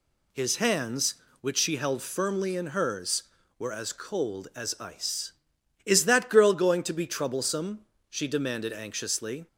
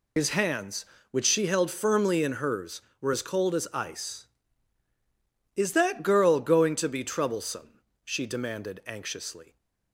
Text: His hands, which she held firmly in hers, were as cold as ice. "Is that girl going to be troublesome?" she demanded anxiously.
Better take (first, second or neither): first